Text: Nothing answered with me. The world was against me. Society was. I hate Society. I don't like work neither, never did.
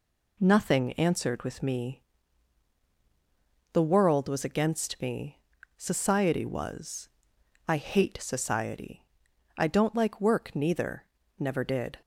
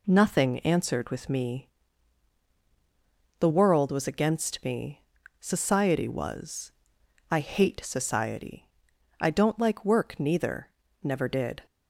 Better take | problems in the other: neither | none

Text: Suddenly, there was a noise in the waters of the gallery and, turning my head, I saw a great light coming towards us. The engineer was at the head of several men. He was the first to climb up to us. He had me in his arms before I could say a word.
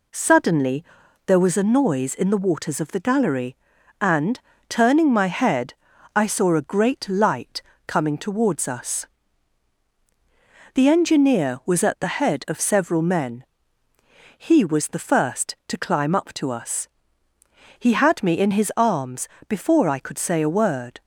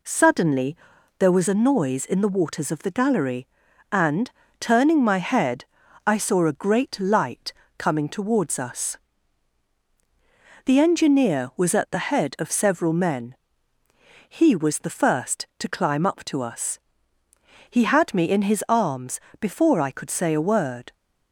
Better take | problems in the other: neither | pauses between "light" and "coming"; slight; the same in both // pauses between "arms" and "before"; slight; the same in both

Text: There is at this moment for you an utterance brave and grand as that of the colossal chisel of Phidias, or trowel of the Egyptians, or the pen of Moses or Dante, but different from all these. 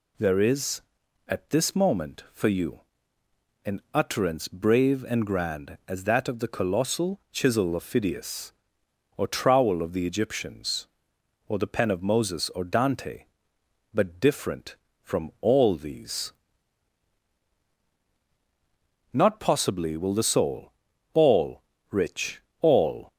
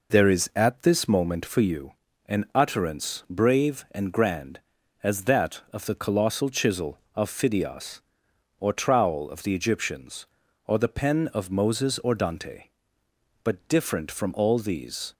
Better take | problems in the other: second | pauses between "you" and "an"; noticeable; at 2.8 s; 0.84 s long; slight in the second // goes on to say "Not possibly will the soul all rich all"; strong; from 19.1 s on; 4.0 s long

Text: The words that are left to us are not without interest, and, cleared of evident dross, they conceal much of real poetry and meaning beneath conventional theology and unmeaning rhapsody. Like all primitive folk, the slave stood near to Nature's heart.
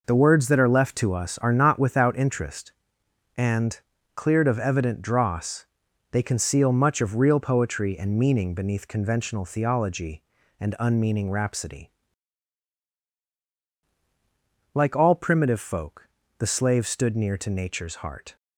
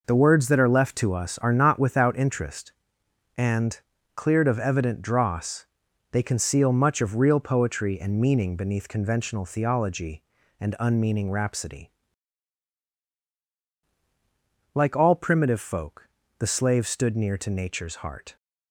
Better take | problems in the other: neither | none

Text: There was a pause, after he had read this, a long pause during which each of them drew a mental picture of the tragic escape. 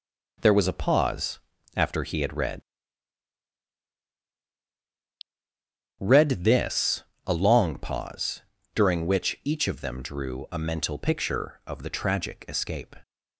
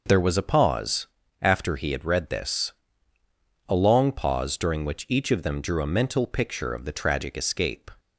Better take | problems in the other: second | says "read" twice; at 5.9 s // pauses between "pause" and "during"; slight; at 8.4 s; 0.32 s long

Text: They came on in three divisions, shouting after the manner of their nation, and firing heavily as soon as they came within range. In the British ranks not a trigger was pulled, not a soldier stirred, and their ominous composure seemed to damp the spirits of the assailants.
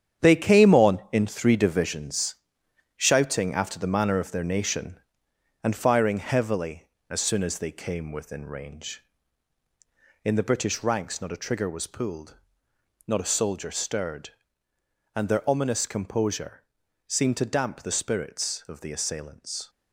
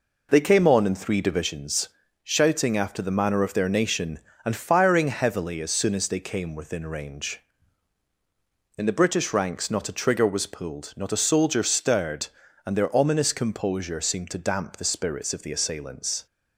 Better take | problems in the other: second | gets quieter; strong; throughout; 9 dB // pauses between "composure" and "seemed"; at 16.6 s; 0.44 s long

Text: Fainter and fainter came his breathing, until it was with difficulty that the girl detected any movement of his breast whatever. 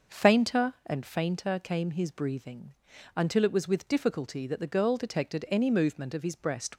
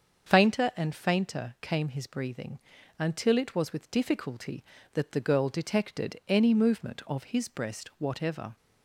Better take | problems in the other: second | starts louder than the rest; noticeable; until 1.2 s; 6 dB; also in the second // stops before "whatever"; at 6.7 s

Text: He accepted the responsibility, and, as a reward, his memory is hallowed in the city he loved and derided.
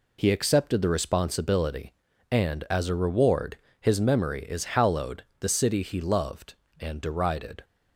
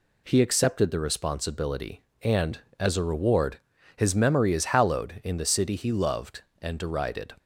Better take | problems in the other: second | skips "in"; at 5.3 s

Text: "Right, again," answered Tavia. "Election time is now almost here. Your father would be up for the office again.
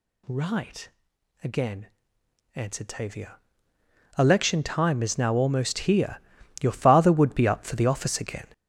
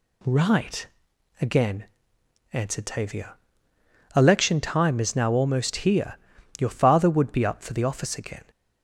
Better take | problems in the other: second | gets louder; strong; throughout; 9 dB

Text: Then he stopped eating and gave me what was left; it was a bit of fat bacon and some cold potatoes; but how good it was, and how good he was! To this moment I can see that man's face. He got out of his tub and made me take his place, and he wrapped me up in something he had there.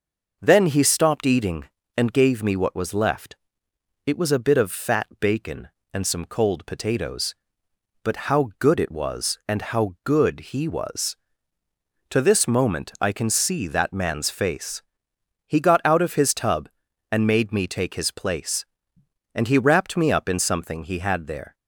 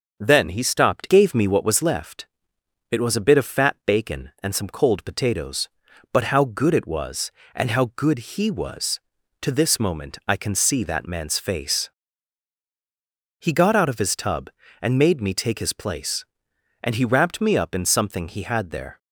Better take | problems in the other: first | starts louder than the rest; until 1.2 s; 6.5 dB // skips "eating and"; at 1.0 s

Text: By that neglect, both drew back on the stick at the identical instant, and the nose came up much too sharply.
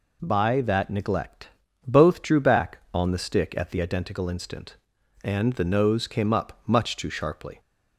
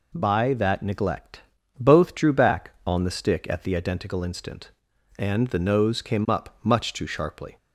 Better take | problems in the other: neither | none

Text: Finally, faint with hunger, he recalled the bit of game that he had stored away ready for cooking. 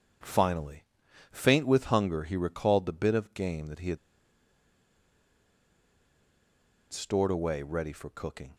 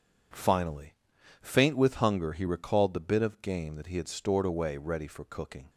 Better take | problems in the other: second | pauses between "had" and "stored"; strong; at 3.9 s; 2.9 s long

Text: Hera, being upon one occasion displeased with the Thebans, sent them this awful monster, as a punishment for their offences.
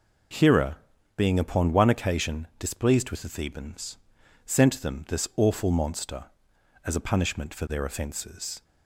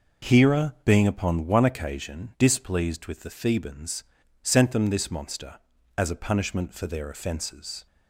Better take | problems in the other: first | skips "awful"; at 5.1 s

